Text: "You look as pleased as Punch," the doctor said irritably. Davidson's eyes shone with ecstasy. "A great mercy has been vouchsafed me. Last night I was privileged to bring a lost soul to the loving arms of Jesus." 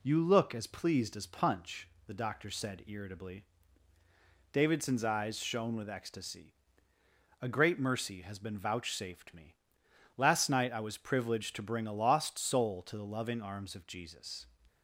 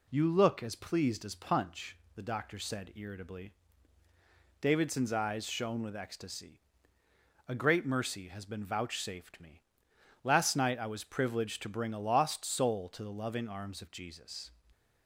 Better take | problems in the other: neither | none

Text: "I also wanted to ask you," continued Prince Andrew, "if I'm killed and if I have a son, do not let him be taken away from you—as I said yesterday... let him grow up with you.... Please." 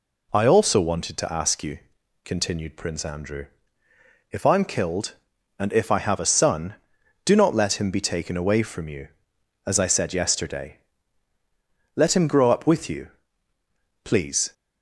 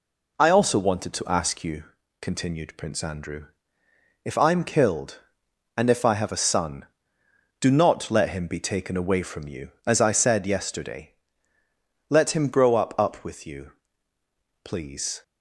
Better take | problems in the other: first | says "up" twice; at 12.9 s

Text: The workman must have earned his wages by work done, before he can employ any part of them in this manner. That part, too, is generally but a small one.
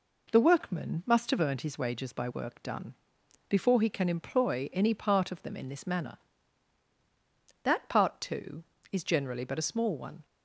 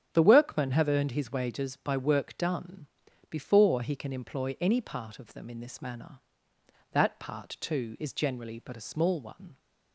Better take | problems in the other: first | starts louder than the rest; strong; until 1.1 s; 8 dB // skips "must"; at 0.7 s

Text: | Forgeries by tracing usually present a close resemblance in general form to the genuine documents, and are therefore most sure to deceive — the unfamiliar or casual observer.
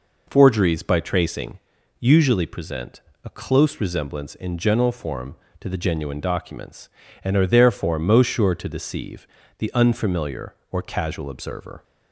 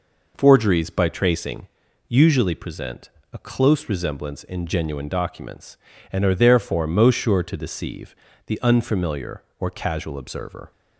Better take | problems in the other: first | pauses between "tracing" and "usually"; at 1.6 s; 0.42 s long; also in the first // pauses between "present" and "a"; slight; at 3.0 s; 0.24 s long; slight in the first // skips "general form to the"; at 4.6 s

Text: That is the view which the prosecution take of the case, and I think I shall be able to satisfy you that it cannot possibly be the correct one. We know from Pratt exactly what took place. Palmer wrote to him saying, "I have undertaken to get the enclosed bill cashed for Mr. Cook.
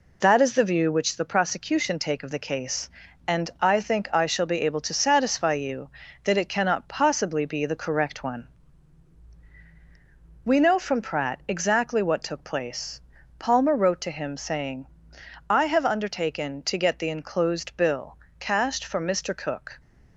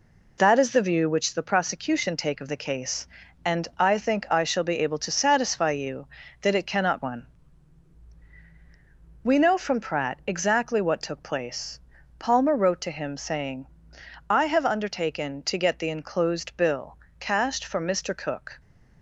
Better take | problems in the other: first | skips "possibly be the correct"; at 7.0 s // pauses between "bill" and "cashed"; slight; at 16.9 s; 0.22 s long; slight in the first

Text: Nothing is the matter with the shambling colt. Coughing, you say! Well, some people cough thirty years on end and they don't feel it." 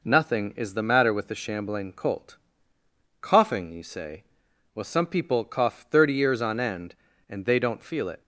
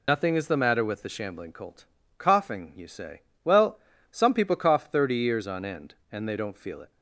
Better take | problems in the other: first | loses the start of "Nothing"; at 0.0 s; 55 ms

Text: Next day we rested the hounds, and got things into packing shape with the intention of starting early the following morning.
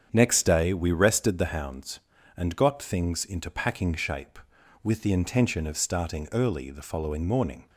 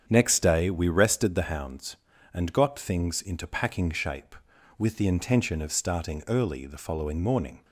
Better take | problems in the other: neither | starts louder than the rest; strong; the same in both

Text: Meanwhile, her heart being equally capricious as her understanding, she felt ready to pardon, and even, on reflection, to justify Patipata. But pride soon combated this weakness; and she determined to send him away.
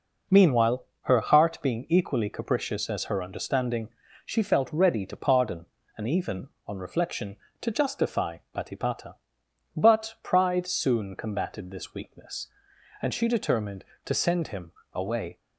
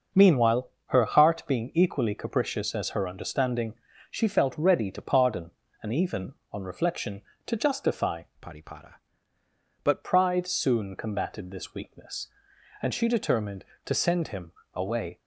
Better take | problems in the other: first | starts louder than the rest; noticeable; until 1.3 s; 6 dB // changes voice from "Patipata" to "But"; from 8.4 to 10.0 s; 1.6 s long // pauses between "him" and "away"; slight; at 14.5 s; 0.20 s long; slight in the first

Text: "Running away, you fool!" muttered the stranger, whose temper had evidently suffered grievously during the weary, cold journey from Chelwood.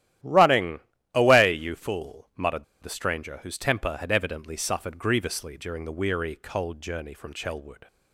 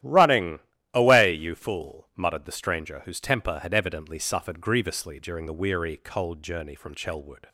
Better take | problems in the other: second | starts louder than the rest; strong; until 1.5 s; 12.5 dB; strong in the second // pauses between "Running" and "away"; slight; at 0.7 s; 0.34 s long; slight in the second // pauses between "muttered" and "the"; slight; at 2.6 s; 0.18 s long

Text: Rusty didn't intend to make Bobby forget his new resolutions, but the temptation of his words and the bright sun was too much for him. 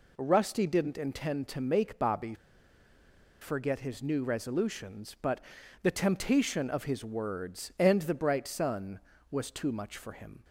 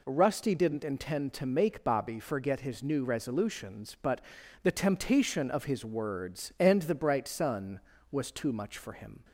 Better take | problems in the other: second | pauses between "Bobby" and "forget"; at 2.3 s; 1.0 s long // pauses between "but" and "the"; at 5.4 s; 0.42 s long; also in the second

